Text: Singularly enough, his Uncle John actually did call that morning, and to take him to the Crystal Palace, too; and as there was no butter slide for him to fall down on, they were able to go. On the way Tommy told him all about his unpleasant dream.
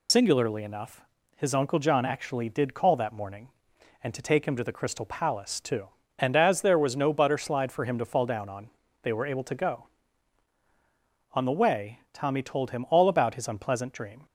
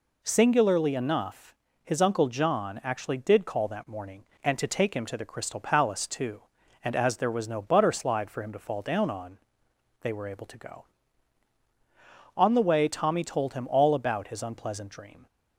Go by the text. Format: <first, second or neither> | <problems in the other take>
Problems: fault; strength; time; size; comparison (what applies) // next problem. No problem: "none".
second | loses the start of "Singularly"; at 0.0 s; 80 ms